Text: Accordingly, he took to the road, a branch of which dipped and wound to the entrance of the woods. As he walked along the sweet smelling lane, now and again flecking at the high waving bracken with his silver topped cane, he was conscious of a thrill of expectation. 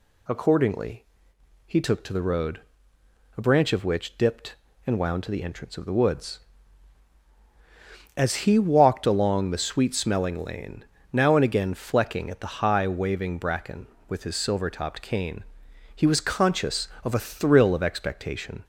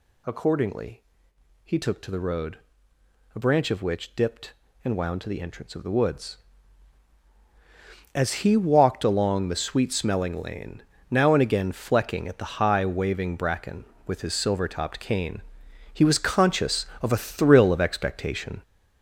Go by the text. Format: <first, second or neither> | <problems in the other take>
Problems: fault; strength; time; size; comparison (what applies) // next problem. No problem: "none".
first | gets louder; throughout; 6.5 dB